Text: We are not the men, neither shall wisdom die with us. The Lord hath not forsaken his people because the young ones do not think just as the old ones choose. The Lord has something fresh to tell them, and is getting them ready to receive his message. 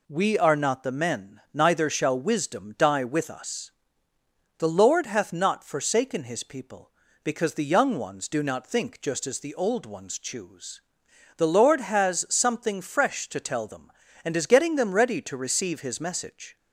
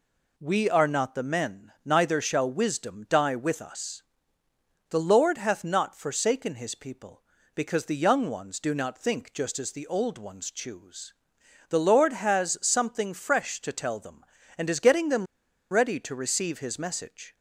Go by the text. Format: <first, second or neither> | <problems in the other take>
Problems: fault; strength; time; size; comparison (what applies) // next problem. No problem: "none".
first | pauses between "them" and "ready"; at 15.2 s; 0.45 s long